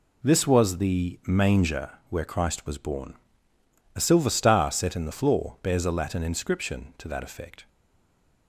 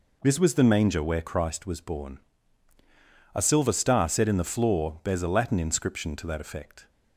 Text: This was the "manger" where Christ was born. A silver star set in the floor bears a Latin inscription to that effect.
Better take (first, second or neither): second